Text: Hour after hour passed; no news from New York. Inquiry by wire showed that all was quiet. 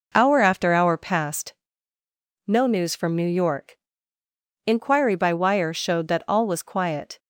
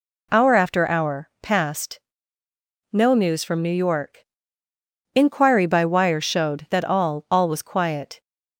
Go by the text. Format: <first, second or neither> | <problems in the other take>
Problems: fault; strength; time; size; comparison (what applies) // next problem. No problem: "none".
first | says "all" twice; at 7.3 s